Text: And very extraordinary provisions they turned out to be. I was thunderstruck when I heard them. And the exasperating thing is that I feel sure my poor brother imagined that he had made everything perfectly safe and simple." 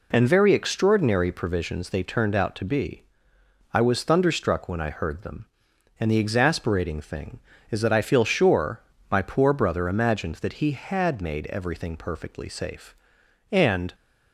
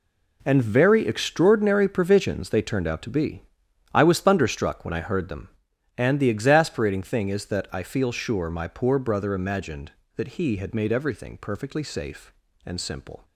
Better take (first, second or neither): second